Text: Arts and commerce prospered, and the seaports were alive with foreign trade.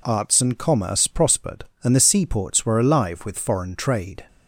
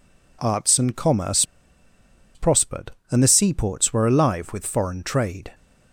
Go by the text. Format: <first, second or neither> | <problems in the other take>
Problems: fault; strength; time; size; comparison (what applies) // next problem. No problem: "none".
first | pauses between "commerce" and "prospered"; noticeable; at 1.4 s; 0.91 s long